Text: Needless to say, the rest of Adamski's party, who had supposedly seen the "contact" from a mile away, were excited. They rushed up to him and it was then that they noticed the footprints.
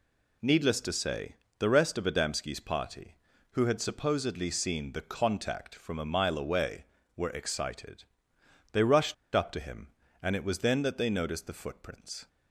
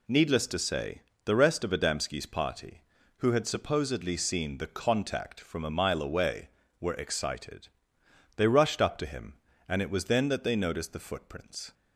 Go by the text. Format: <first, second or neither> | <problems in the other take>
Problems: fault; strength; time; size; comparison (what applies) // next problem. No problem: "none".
second | pauses between "rushed" and "up"; slight; at 9.1 s; 0.20 s long